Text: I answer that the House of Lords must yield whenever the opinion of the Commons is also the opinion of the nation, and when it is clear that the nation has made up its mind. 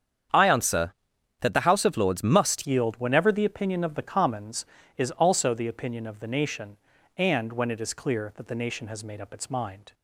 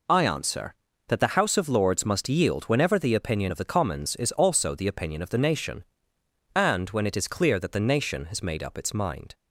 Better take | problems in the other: second | starts louder than the rest; strong; until 1.7 s; 8 dB // changes voice at "yield"; from 2.6 s on; 7.3 s long

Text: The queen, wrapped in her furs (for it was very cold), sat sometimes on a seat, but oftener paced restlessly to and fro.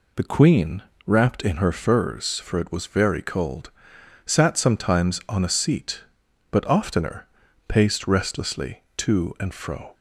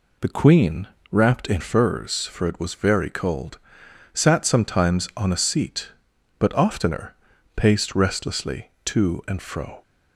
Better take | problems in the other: first | skips "her"; at 1.6 s // pauses between "oftener" and "paced"; at 7.1 s; 0.42 s long; also in the first

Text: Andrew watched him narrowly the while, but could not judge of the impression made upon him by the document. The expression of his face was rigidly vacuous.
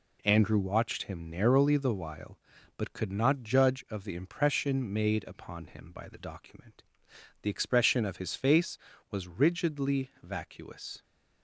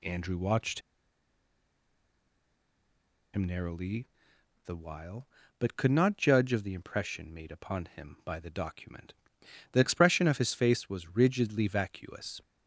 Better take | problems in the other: first | pauses between "watched" and "him"; strong; at 0.8 s; 2.5 s long // pauses between "narrowly" and "the"; noticeable; at 4.0 s; 0.56 s long

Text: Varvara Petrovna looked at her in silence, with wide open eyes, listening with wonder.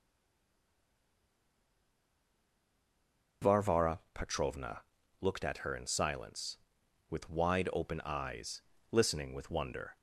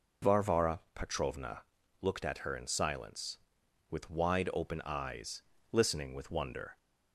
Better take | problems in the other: second | stays silent before the first word; strong; until 3.4 s; 3.4 s long // pauses between "Varvara" and "Petrovna"; slight; at 3.9 s; 0.16 s long; slight in the second // pauses between "Petrovna" and "looked"; at 4.8 s; 0.38 s long; also in the second

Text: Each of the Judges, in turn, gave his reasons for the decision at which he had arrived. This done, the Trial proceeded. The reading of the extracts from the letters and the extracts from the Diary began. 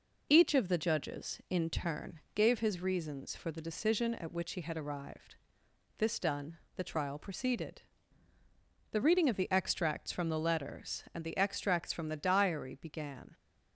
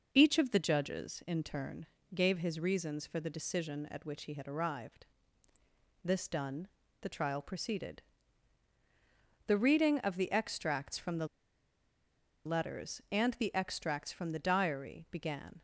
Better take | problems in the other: first | pauses between "the" and "letters"; at 11.2 s; 1.1 s long

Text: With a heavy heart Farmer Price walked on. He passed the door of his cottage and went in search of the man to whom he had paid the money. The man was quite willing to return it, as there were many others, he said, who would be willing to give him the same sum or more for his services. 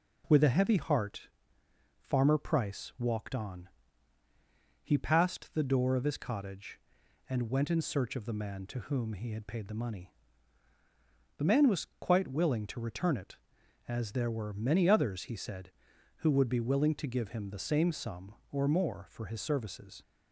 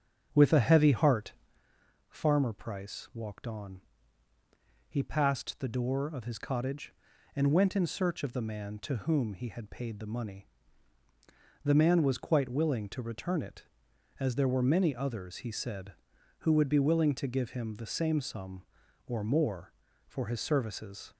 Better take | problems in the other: first | starts louder than the rest; strong; until 1.6 s; 7.5 dB // pauses between "heart" and "Farmer"; noticeable; at 1.3 s; 0.76 s long; noticeable in the first

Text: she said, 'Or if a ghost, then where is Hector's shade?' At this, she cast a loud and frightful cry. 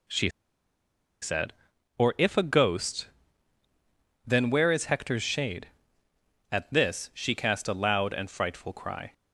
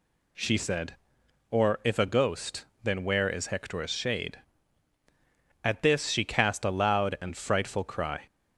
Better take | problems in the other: second | pauses between "she" and "said"; noticeable; at 0.3 s; 0.91 s long

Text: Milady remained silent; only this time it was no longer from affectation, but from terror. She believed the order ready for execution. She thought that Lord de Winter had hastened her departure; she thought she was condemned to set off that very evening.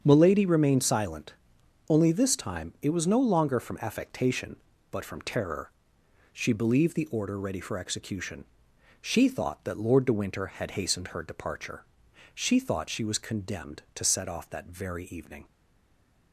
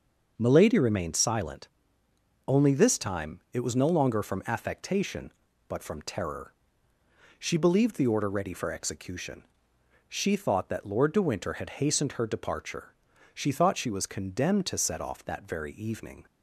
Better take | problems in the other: second | starts louder than the rest; strong; until 1.0 s; 7 dB; noticeable in the second // stays silent after the last word; slight; from 15.4 s on; 0.9 s long

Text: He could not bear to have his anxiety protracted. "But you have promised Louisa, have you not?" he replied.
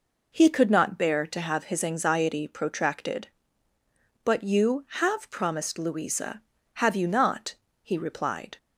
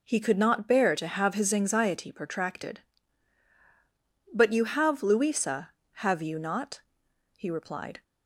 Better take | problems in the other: first | skips "promised"; at 5.0 s

